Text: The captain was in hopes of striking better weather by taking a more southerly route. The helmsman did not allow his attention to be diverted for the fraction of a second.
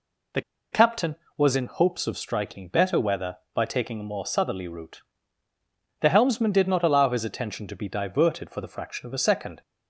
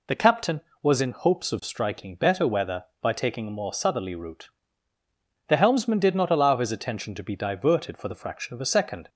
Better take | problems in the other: second | pauses between "The" and "captain"; slight; at 0.4 s; 0.31 s long

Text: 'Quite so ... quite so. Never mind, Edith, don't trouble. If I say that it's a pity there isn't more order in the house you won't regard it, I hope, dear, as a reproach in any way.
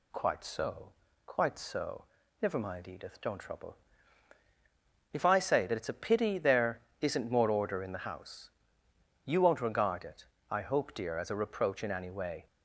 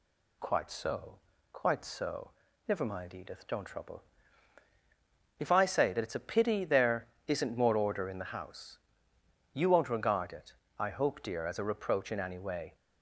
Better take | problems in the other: neither | pauses between "there" and "isn't"; slight; the same in both // pauses between "house" and "you"; noticeable; the same in both

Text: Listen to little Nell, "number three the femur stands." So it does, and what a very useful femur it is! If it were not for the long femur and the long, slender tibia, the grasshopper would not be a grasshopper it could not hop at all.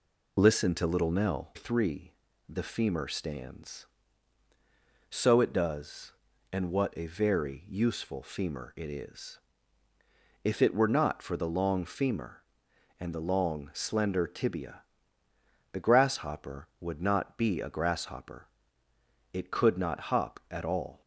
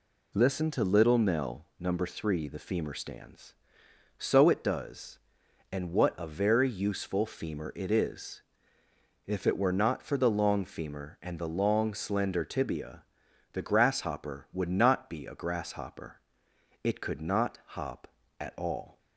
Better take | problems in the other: second | skips "number"; at 1.5 s // pauses between "three" and "the"; at 2.1 s; 0.38 s long // pauses between "grasshopper" and "it"; noticeable; at 18.4 s; 0.84 s long; noticeable in the second

